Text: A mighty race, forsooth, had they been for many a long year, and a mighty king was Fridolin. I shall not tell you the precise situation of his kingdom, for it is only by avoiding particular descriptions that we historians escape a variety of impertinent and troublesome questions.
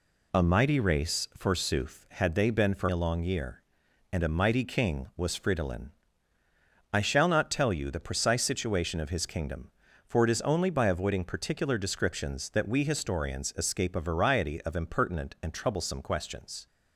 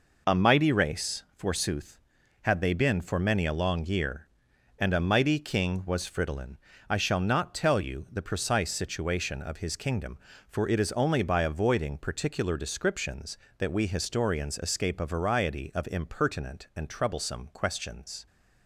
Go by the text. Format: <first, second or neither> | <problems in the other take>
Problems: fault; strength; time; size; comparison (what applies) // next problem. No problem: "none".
second | skips "many"; at 2.8 s